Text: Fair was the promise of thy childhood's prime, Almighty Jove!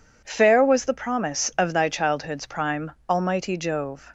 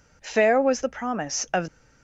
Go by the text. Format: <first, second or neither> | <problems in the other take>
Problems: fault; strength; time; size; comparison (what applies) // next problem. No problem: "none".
first | stops before "thy childhood's prime Almighty Jove"; at 1.6 s